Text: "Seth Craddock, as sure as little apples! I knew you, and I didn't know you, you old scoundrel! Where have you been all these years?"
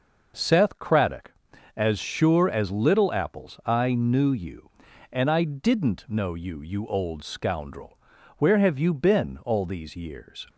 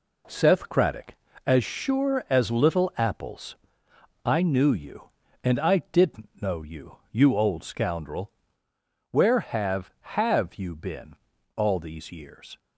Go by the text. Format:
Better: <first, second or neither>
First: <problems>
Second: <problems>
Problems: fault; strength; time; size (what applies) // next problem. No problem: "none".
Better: first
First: none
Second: says "have" twice; at 9.9 s // pauses between "been" and "all"; at 11.1 s; 0.40 s long